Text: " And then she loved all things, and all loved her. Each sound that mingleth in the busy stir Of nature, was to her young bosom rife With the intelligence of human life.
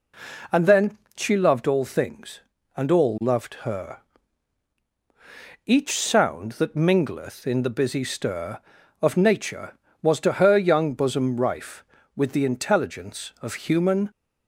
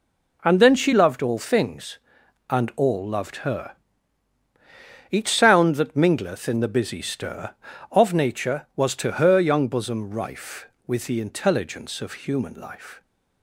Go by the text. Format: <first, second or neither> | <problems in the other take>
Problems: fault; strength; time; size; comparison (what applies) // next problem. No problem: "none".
second | pauses between "then" and "she"; slight; at 0.9 s; 0.20 s long // stops before "life"; at 14.0 s